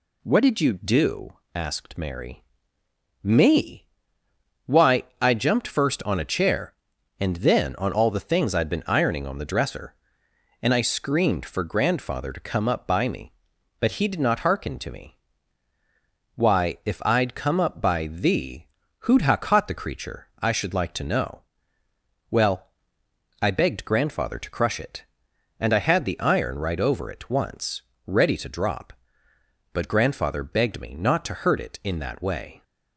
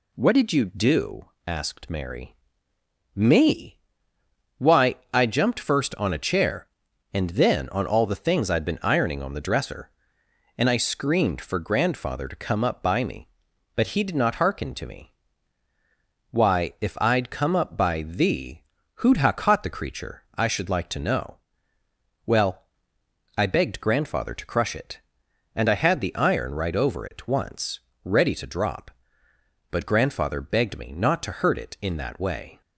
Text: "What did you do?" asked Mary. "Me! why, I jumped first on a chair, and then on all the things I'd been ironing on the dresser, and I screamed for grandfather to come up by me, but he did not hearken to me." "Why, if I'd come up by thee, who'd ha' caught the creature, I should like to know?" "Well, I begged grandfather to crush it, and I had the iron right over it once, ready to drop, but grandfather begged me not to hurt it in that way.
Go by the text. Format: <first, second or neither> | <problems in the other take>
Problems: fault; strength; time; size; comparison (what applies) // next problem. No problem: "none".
neither | none